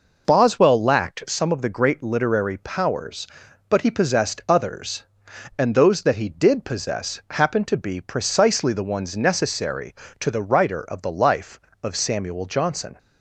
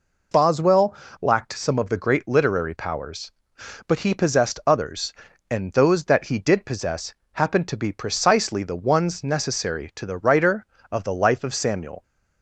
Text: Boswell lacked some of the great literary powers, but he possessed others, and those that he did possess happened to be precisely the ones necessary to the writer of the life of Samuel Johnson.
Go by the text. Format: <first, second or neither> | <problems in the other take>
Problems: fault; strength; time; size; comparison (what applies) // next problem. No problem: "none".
first | pauses between "Boswell" and "lacked"; slight; at 0.9 s; 0.26 s long // pauses between "possess" and "happened"; slight; at 7.1 s; 0.20 s long // stops before "Johnson"; at 12.0 s